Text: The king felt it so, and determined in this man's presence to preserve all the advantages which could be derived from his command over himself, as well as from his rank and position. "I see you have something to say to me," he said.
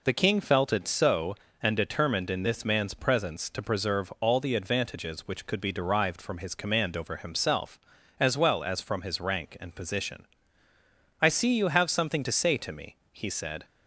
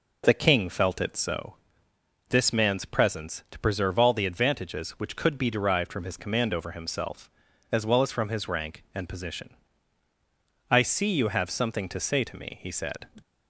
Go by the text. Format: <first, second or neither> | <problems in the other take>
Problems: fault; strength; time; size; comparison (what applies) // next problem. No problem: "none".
first | skips "and determined in"; at 1.9 s